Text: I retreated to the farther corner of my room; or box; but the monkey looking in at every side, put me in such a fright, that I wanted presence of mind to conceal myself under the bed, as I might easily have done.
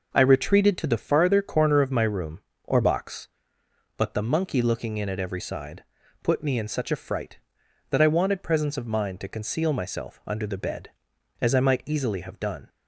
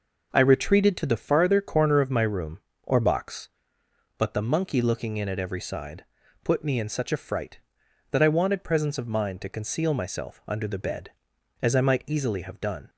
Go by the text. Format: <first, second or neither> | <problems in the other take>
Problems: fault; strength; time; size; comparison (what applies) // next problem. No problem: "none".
neither | none